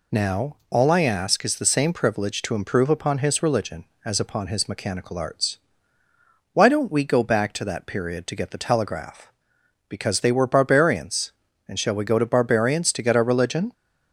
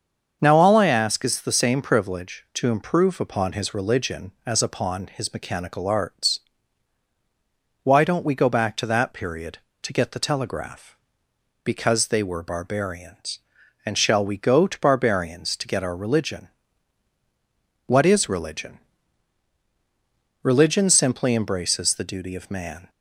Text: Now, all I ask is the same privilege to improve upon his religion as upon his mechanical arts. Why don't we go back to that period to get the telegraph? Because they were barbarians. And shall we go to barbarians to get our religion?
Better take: first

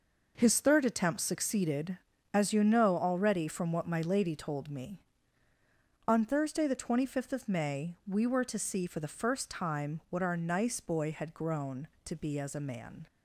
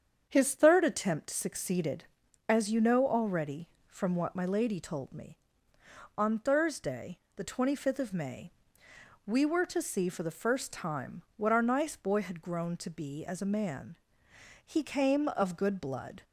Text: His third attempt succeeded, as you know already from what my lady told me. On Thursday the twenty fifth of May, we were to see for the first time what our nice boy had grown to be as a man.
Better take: first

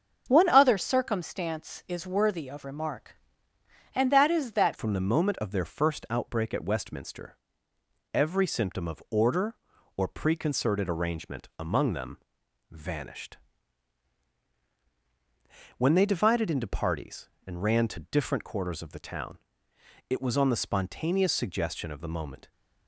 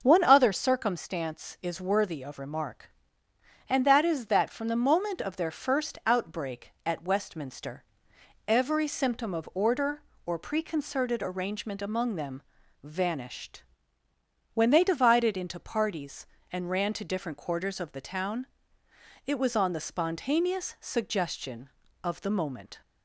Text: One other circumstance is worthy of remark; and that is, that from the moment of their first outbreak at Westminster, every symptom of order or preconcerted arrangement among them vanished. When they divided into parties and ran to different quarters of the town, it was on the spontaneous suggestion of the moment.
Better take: second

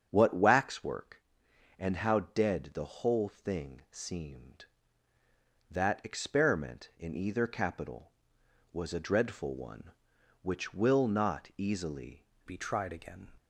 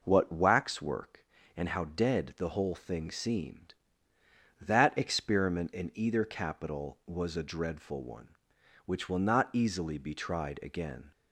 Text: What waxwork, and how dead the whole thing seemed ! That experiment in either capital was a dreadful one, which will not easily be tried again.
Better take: second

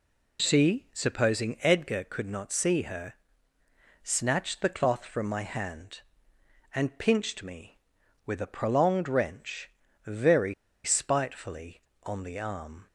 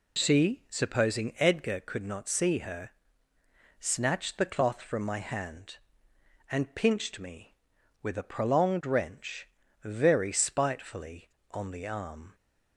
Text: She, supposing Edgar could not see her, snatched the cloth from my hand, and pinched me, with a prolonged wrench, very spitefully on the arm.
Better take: second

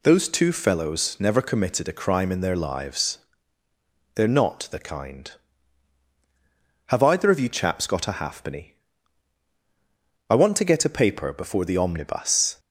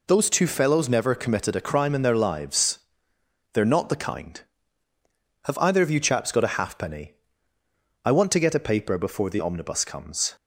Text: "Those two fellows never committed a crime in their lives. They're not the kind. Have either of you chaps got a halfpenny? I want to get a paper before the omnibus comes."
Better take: second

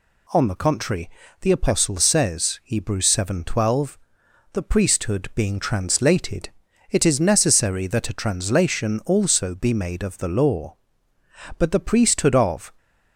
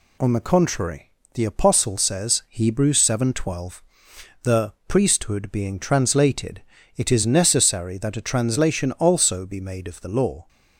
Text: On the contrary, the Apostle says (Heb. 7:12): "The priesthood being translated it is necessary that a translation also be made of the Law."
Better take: second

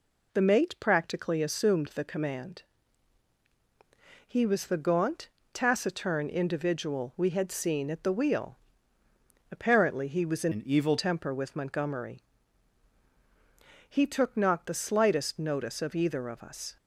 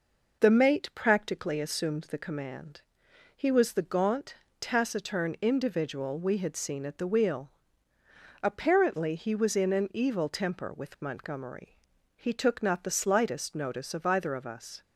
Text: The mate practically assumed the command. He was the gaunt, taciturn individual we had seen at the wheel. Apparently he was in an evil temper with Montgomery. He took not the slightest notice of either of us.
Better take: second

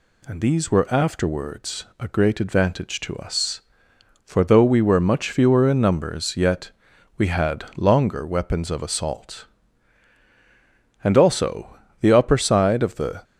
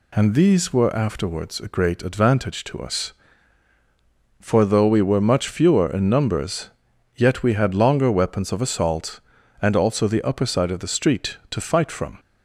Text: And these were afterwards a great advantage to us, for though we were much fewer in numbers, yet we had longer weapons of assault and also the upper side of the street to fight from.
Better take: second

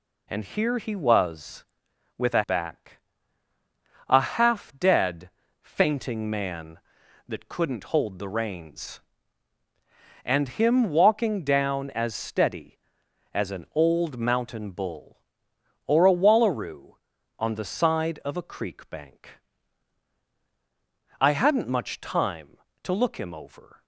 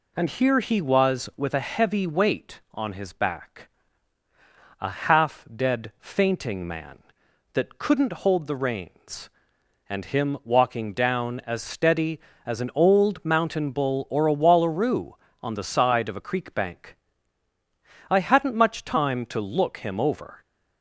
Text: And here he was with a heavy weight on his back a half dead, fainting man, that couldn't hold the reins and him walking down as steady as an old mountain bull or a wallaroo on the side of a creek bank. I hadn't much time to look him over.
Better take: second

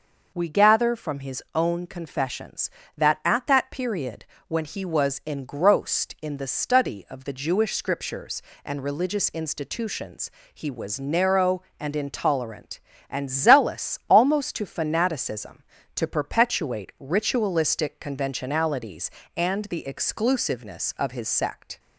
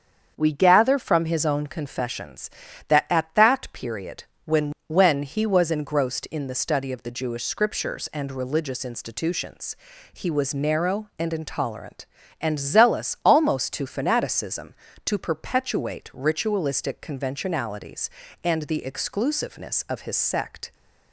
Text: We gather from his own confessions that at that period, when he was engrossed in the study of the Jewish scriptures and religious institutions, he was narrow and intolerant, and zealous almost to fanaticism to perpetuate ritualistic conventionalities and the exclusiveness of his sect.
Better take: first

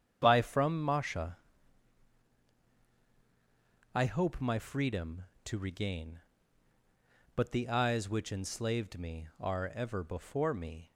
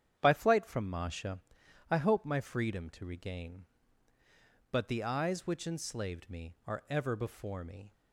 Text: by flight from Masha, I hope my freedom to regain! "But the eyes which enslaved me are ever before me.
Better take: second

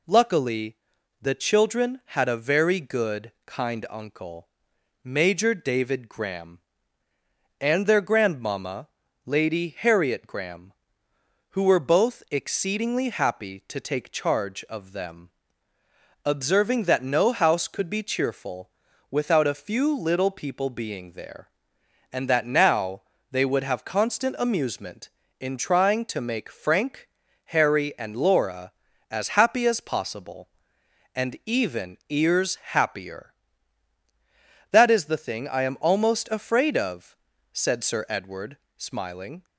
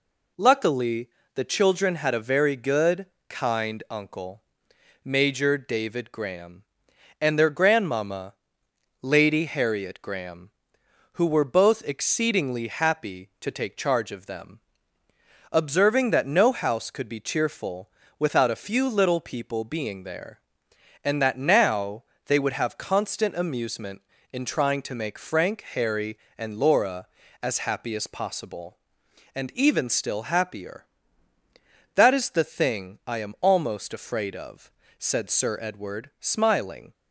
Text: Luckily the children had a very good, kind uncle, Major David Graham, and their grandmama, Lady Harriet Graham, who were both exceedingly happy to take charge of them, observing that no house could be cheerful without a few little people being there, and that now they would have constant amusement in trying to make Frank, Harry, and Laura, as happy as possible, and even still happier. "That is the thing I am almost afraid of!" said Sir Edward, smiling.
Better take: second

